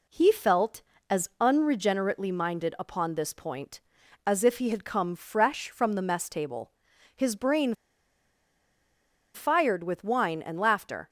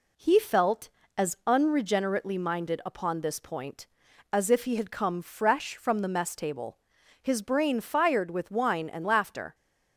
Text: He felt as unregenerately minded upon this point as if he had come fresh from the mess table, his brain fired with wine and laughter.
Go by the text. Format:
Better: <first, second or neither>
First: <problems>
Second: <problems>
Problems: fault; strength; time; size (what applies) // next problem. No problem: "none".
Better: second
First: pauses between "brain" and "fired"; strong; at 7.7 s; 1.6 s long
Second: none